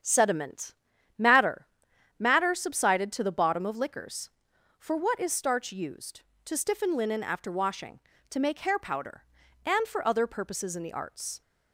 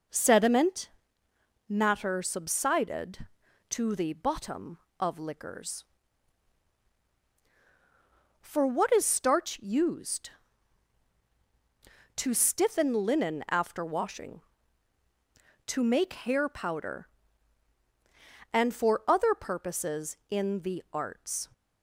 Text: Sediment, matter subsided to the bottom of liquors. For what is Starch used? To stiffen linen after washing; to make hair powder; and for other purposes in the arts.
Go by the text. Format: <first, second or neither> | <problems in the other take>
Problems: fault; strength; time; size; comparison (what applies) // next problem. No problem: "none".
second | starts louder than the rest; strong; until 1.4 s; 8 dB // says "matter" twice; at 2.1 s